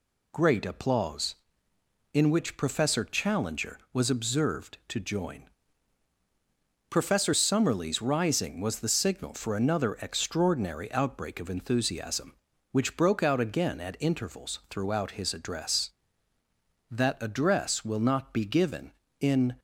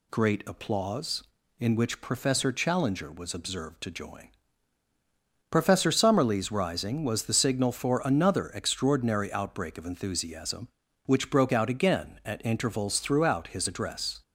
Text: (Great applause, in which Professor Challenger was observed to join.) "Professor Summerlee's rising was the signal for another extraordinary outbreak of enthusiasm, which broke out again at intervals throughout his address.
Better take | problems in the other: second | goes on to say "That address will not be given in"; strong; from 16.9 s on; 2.6 s long

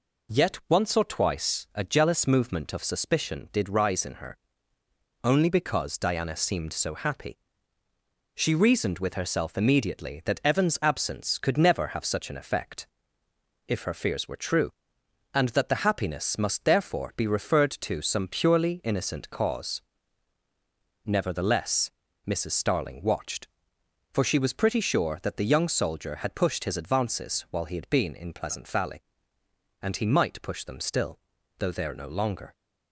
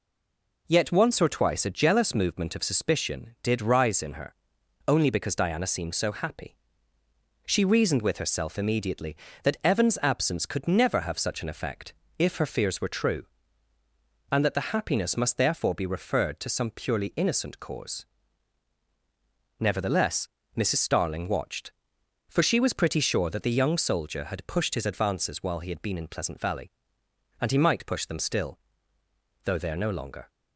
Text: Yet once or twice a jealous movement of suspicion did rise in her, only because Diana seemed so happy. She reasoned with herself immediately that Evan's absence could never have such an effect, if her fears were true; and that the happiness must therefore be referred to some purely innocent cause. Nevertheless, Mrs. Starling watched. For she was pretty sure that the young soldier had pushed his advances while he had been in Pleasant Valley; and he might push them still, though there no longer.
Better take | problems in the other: first | stays silent before the first word; slight; until 0.6 s; 0.6 s long

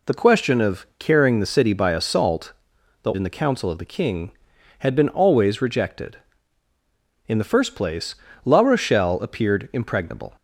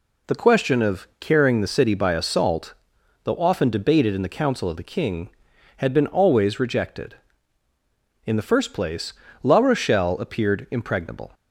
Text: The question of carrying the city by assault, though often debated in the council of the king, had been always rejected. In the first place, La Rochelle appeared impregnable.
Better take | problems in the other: second | skips "often debated"; at 3.1 s

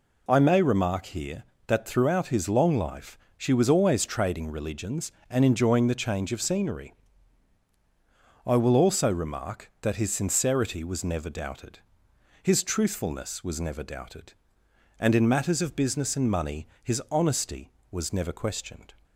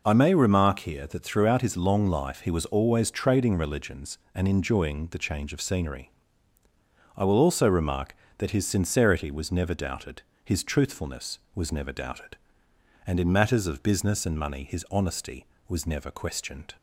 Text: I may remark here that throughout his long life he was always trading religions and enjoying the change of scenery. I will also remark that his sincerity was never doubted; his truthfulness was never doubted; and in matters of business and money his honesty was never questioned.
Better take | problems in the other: second | says "she" for "he"; at 3.3 s // pauses between "money" and "his"; slight; at 16.6 s; 0.16 s long

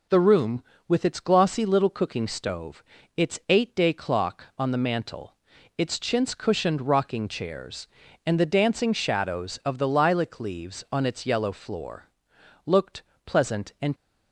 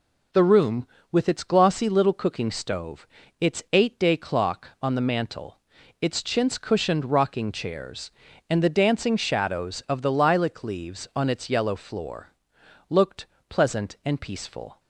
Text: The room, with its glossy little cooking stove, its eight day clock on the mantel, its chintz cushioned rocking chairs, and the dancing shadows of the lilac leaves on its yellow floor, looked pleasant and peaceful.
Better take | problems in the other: second | pauses between "looked" and "pleasant"; slight; at 13.0 s; 0.24 s long; slight in the second // stops before "peaceful"; at 13.9 s

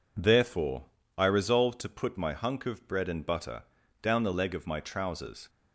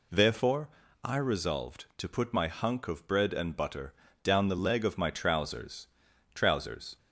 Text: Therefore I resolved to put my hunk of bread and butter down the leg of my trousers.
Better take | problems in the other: first | pauses between "Therefore" and "I"; slight; at 0.6 s; 0.34 s long; slight in the first // pauses between "butter" and "down"; slight; at 3.9 s; 0.30 s long; slight in the first // says "trousers" twice; at 6.3 s

